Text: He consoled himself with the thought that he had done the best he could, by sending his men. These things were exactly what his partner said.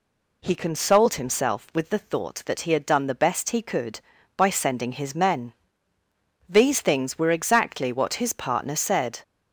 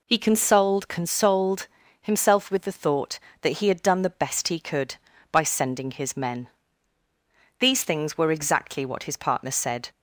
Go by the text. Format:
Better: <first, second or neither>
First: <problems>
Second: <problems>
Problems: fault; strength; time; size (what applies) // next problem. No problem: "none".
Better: first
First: none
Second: says "consoled" twice; at 0.8 s